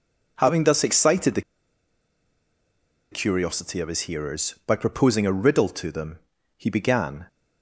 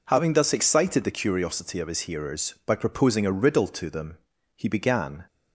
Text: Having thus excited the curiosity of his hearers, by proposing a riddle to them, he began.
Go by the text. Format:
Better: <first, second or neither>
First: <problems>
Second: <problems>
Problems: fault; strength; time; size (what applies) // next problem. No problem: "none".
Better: second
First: pauses between "the" and "curiosity"; strong; at 1.4 s; 1.7 s long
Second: none